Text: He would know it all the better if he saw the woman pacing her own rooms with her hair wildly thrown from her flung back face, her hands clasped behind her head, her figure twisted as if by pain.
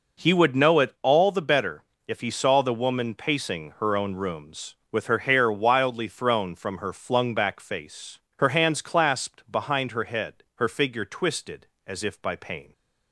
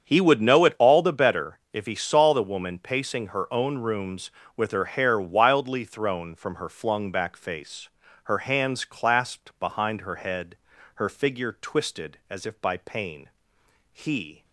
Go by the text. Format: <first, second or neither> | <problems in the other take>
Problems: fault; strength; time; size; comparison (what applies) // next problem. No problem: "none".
first | starts louder than the rest; strong; until 1.0 s; 7.5 dB // pauses between "better" and "if"; slight; at 1.5 s; 0.16 s long; slight in the first // goes on to say "He"; from 13.9 s on; 0.52 s long